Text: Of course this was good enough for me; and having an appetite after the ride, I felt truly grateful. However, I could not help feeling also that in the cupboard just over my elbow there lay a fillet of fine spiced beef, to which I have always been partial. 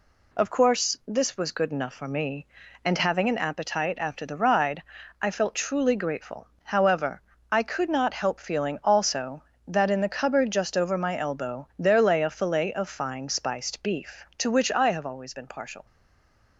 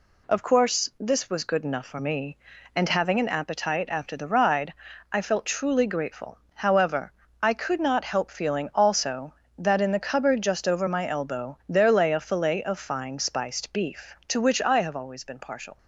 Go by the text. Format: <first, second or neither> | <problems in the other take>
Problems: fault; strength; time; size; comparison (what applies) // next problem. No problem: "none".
second | stays silent after the last word; slight; from 15.8 s on; 0.7 s long